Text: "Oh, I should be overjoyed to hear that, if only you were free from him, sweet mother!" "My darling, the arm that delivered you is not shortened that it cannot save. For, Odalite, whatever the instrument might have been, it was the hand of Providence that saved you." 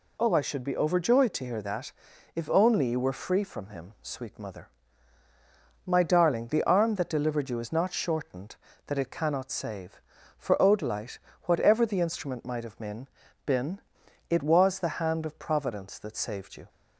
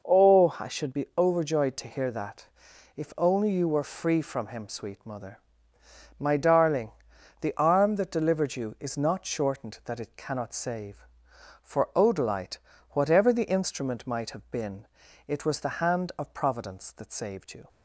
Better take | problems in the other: second | says "been" twice; at 13.4 s

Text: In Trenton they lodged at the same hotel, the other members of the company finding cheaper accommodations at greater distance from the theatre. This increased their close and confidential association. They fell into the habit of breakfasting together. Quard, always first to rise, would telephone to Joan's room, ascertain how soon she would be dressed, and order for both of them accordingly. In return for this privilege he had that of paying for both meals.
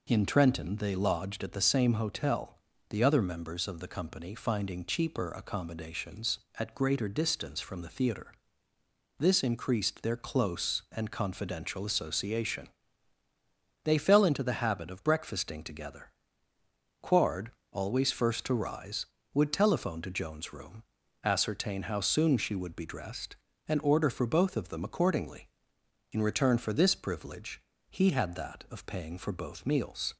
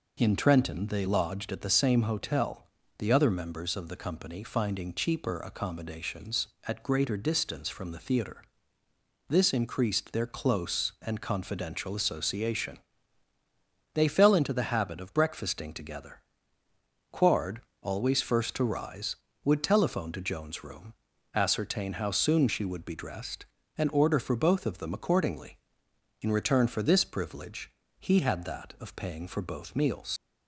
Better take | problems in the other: first | pauses between "privilege" and "he"; slight; at 27.6 s; 0.28 s long; slight in the first // leaves "meals" unfinished; at 30.1 s; 90 ms

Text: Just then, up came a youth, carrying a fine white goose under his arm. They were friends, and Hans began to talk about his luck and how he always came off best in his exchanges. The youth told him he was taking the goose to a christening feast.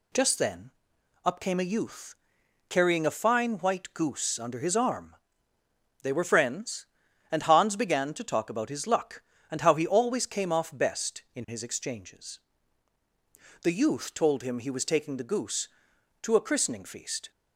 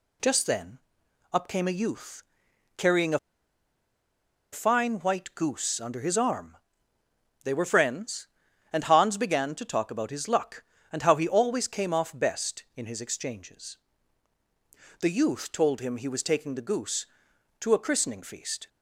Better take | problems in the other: first | pauses between "a" and "fine"; strong; at 3.1 s; 1.3 s long

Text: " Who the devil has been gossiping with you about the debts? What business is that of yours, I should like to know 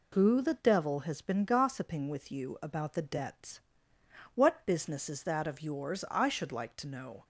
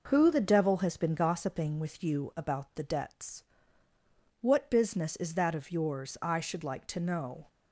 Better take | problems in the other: neither | none

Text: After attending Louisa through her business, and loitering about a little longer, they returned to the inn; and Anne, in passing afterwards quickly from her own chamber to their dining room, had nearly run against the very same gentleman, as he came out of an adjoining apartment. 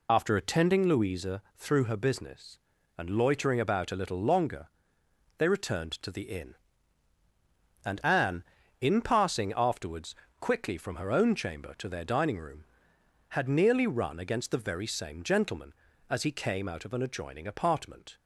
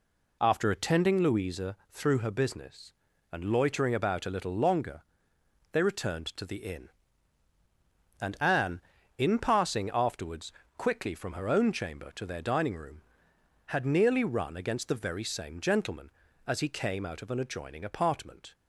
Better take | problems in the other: second | loses the start of "After"; at 0.0 s; 40 ms // pauses between "afterwards" and "quickly"; slight; at 10.1 s; 0.24 s long; slight in the second

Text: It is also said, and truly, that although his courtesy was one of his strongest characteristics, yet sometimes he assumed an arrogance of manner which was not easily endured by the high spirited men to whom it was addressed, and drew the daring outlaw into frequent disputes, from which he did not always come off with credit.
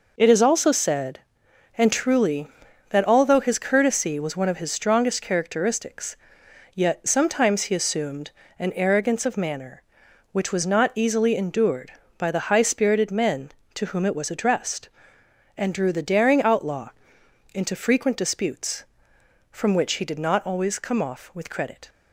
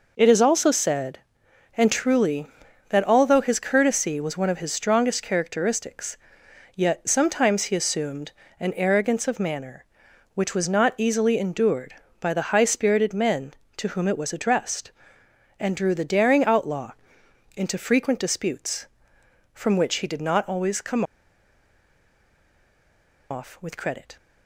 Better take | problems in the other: first | pauses between "assumed" and "an"; slight; at 8.3 s; 0.28 s long; slight in the first // pauses between "outlaw" and "into"; noticeable; at 16.9 s; 0.64 s long; noticeable in the first // pauses between "come" and "off"; strong; at 21.0 s; 2.2 s long

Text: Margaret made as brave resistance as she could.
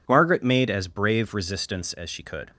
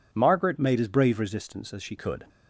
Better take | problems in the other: first | changes voice from "made" to "she"; from 0.5 to 1.9 s; 1.4 s long

